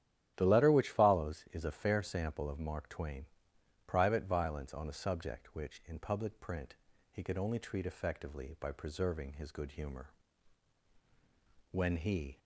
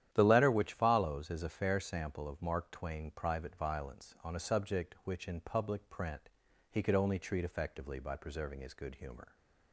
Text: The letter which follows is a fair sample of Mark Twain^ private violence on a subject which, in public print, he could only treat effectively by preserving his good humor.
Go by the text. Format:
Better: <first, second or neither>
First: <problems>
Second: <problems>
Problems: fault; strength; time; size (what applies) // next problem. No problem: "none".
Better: second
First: starts louder than the rest; strong; until 1.3 s; 12 dB // pauses between "Twain" and "private"; noticeable; at 3.2 s; 0.60 s long // goes on to say "When he"; noticeable; from 11.7 s on; 0.68 s long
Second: starts louder than the rest; strong; until 1.1 s; 11 dB